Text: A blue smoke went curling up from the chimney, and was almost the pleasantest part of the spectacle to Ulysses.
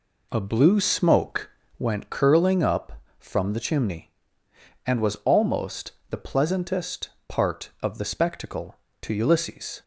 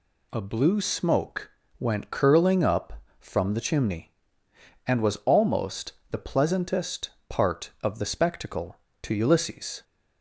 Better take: second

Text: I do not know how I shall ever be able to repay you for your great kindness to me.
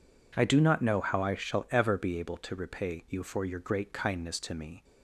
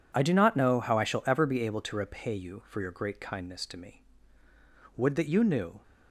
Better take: first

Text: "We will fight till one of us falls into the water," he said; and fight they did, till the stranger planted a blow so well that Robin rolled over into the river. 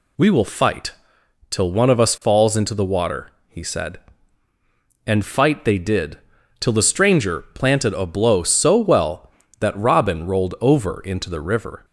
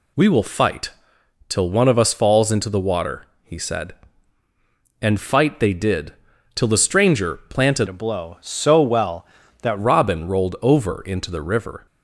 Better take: first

